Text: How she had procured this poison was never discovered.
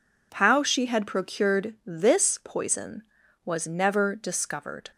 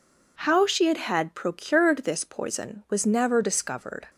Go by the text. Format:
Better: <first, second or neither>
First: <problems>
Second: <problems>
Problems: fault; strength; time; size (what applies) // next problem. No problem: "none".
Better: first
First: none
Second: says "had" twice; at 0.9 s